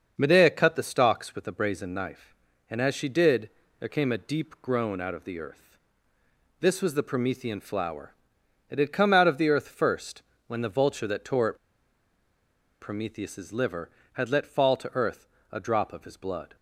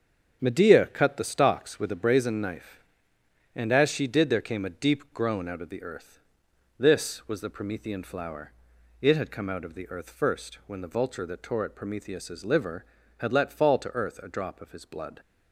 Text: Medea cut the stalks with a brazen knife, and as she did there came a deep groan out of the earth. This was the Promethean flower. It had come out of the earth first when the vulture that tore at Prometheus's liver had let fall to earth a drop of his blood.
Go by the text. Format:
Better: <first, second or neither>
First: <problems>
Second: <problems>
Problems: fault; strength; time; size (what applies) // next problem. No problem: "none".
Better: second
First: starts louder than the rest; until 1.1 s; 6.5 dB // pauses between "did" and "there"; slight; at 3.5 s; 0.30 s long // pauses between "first" and "when"; slight; at 10.2 s; 0.24 s long // pauses between "at" and "Prometheus's"; at 11.5 s; 1.2 s long // pauses between "earth" and "a"; slight; at 15.2 s; 0.22 s long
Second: starts louder than the rest; until 1.4 s; 7 dB